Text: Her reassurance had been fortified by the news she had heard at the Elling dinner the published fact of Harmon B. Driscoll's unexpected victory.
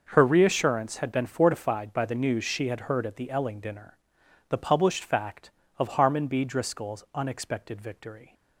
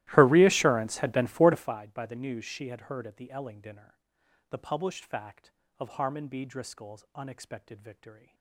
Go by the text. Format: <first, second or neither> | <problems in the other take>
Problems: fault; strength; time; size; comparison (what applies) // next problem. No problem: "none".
first | starts louder than the rest; strong; until 1.8 s; 16 dB // pauses between "dinner" and "the"; noticeable; at 3.9 s; 0.50 s long; noticeable in the first